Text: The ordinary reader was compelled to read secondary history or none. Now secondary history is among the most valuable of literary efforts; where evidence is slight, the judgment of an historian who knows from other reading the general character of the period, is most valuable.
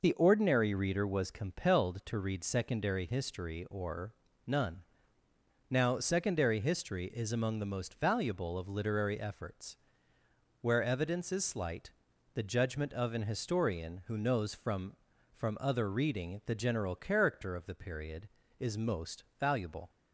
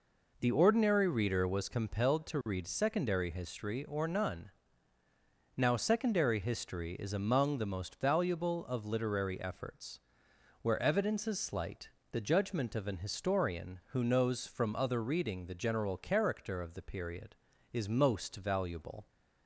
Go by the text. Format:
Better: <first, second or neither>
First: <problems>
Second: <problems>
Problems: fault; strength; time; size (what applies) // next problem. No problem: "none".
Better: second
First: pauses between "or" and "none"; slight; at 4.1 s; 0.32 s long // says "from" twice; at 15.3 s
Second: none